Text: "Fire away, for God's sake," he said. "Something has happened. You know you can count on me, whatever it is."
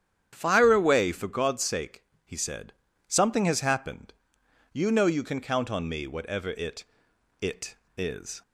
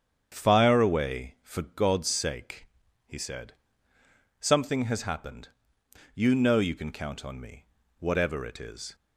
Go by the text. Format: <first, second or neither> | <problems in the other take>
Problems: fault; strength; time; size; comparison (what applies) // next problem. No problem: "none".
second | starts louder than the rest; strong; until 1.3 s; 9.5 dB; strong in the second // says "it" twice; at 7.3 s